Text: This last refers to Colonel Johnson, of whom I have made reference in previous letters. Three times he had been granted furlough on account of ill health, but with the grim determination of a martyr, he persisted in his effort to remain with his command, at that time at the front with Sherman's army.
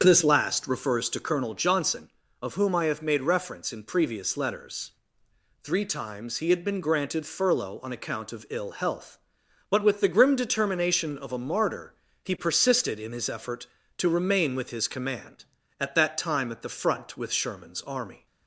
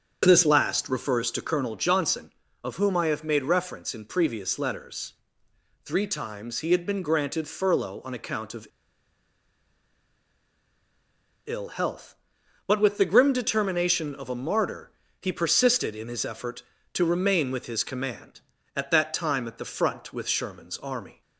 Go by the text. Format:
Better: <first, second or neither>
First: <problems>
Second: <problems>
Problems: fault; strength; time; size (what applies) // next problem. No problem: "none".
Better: first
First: starts louder than the rest; strong; until 1.0 s; 7 dB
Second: starts louder than the rest; strong; until 1.2 s; 7 dB // pauses between "of" and "ill"; strong; at 8.6 s; 2.8 s long